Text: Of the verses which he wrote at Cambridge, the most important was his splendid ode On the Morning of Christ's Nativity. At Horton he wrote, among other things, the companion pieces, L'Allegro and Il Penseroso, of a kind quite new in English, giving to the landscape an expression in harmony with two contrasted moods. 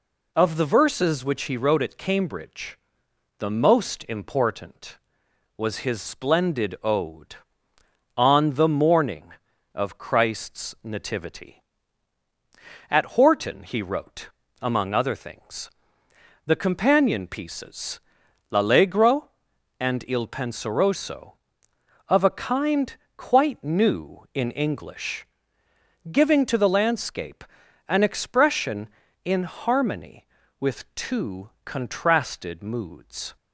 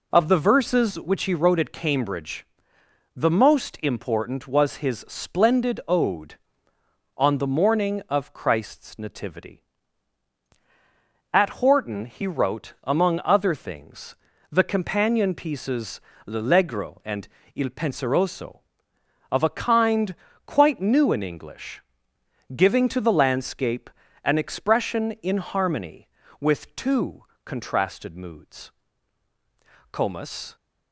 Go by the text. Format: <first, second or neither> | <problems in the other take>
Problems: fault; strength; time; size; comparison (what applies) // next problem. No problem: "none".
first | pauses between "and" and "Il"; slight; at 17.2 s; 0.26 s long // pauses between "kind" and "quite"; slight; at 20.1 s; 0.32 s long; slight in the first // pauses between "landscape" and "an"; slight; at 23.8 s; 0.36 s long; noticeable in the first // pauses between "two" and "contrasted"; slight; at 27.2 s; 0.22 s long; slight in the first // goes on to say "Comus"; noticeable; from 29.9 s on; 0.62 s long